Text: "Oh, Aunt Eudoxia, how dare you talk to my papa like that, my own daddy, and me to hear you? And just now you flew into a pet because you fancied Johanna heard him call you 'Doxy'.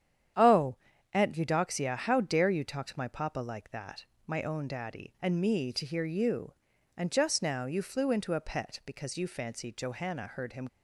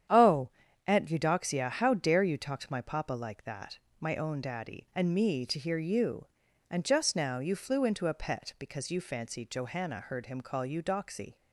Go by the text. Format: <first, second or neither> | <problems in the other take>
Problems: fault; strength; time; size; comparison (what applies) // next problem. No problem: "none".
second | starts louder than the rest; strong; until 1.7 s; 9 dB; strong in the second // stops before "call you Doxy"; at 10.6 s